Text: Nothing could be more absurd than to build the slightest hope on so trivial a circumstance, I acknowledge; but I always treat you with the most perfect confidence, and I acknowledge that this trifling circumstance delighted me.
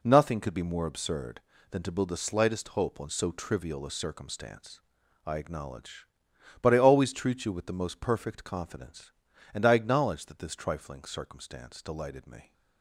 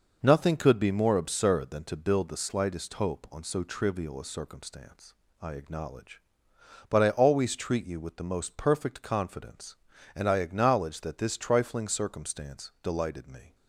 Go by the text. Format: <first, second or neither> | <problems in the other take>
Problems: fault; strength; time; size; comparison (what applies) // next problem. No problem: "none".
neither | none